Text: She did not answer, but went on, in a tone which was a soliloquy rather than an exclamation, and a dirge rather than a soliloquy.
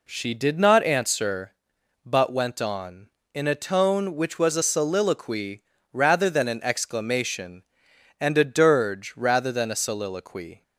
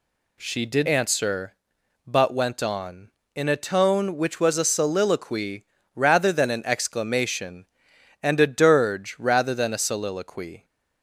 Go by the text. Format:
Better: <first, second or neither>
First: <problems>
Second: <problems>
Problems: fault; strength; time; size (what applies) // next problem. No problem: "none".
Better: first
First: pauses between "soliloquy" and "rather"; slight; at 5.6 s; 0.28 s long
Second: skips "not"; at 0.8 s // pauses between "soliloquy" and "rather"; slight; at 5.6 s; 0.28 s long